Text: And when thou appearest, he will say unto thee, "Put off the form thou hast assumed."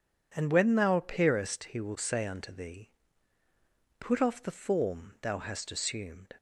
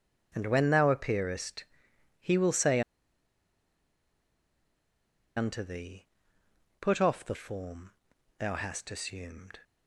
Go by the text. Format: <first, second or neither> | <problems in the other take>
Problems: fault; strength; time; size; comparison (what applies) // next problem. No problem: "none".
first | pauses between "say" and "unto"; strong; at 2.8 s; 2.5 s long // pauses between "form" and "thou"; noticeable; at 7.9 s; 0.48 s long